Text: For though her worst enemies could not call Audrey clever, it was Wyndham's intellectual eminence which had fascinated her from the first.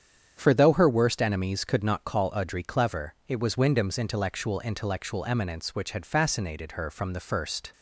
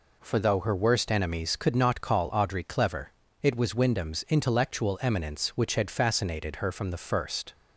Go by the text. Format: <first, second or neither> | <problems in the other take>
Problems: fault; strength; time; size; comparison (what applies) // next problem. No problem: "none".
second | starts louder than the rest; strong; until 1.3 s; 8 dB // says "intellectual" twice; at 4.5 s